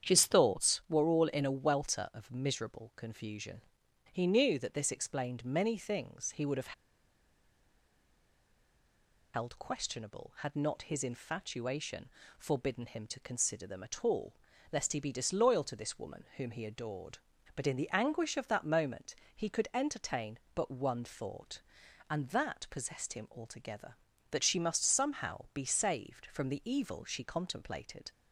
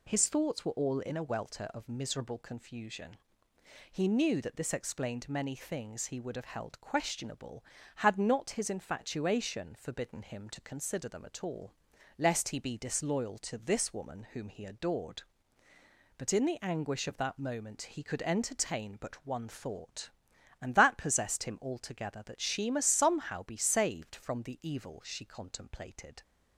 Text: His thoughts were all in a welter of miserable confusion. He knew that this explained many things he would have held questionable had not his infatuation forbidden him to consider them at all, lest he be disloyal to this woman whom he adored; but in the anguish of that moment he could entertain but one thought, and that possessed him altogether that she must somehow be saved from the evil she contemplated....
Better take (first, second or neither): second